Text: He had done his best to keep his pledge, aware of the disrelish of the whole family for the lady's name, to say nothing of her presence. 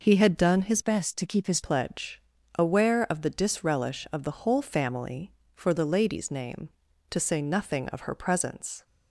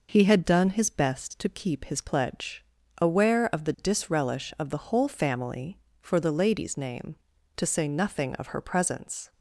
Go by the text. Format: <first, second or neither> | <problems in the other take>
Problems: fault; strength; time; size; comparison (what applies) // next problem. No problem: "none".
second | changes voice from "best" to "his"; from 0.8 to 1.6 s; 0.8 s long